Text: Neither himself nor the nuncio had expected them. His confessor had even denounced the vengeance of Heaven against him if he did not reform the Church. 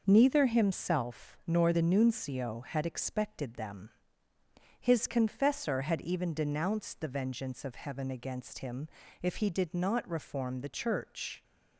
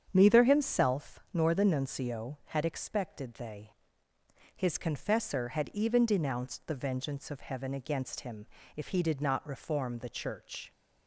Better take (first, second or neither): first